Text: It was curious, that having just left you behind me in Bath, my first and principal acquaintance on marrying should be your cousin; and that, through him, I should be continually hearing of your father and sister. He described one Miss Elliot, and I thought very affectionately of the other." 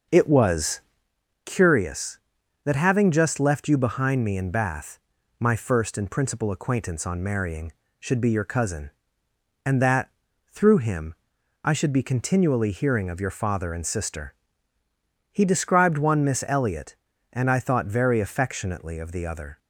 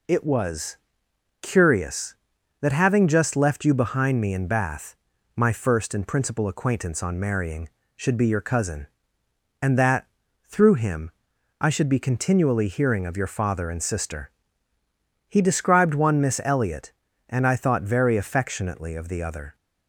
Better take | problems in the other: second | starts louder than the rest; until 1.1 s; 6.5 dB // pauses between "was" and "curious"; noticeable; at 0.8 s; 0.64 s long; noticeable in the second

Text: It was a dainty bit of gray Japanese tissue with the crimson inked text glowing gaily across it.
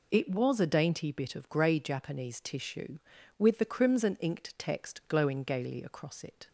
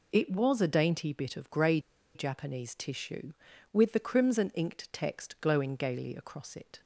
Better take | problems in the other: first | pauses between "gray" and "Japanese"; slight; at 1.7 s; 0.35 s long

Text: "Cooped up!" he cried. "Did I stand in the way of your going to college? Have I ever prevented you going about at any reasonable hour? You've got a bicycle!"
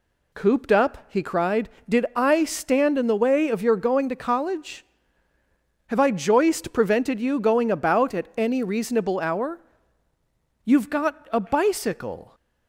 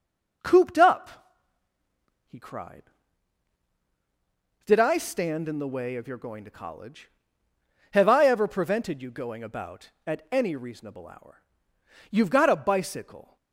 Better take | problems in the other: second | says "joist" for "ever"; at 6.1 s

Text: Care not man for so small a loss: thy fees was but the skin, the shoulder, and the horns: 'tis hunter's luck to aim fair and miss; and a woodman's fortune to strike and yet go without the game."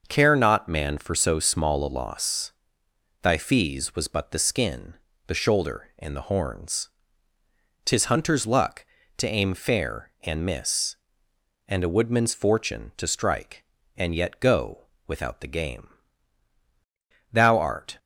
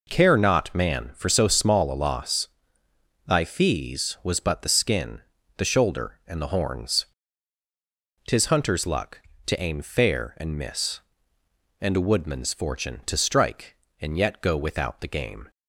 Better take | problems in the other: second | starts louder than the rest; noticeable; until 1.0 s; 6 dB // pauses between "go" and "without"; slight; at 14.8 s; 0.22 s long // goes on to say "Thou art"; noticeable; from 17.3 s on; 0.64 s long

